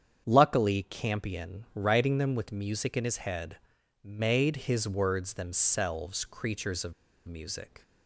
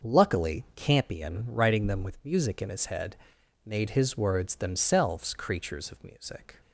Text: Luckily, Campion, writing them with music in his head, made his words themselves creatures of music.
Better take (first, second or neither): second